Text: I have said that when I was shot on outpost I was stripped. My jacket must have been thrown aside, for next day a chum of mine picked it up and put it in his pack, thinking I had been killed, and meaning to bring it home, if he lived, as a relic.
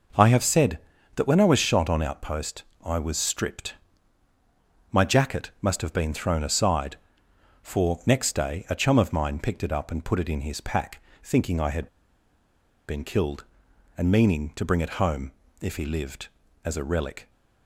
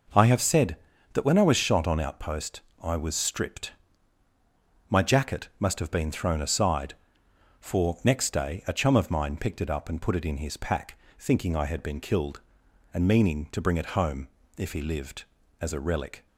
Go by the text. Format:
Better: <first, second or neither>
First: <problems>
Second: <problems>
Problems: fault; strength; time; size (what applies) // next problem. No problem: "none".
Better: second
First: pauses between "outpost" and "I"; slight; at 2.6 s; 0.22 s long // pauses between "had" and "been"; at 11.8 s; 1.0 s long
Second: pauses between "outpost" and "I"; slight; at 2.6 s; 0.22 s long